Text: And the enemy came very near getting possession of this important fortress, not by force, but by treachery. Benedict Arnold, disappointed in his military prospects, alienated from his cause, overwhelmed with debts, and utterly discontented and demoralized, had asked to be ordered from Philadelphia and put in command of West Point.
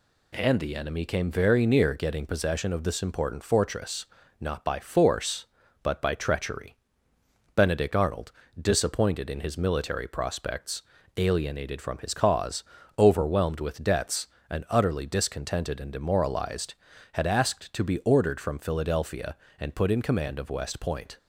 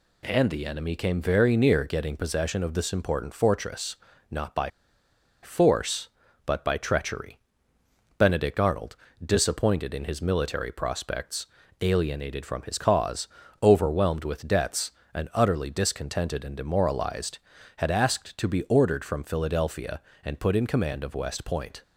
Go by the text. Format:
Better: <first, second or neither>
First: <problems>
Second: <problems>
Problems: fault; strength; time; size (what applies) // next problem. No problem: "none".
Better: first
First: none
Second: pauses between "by" and "force"; noticeable; at 4.6 s; 0.72 s long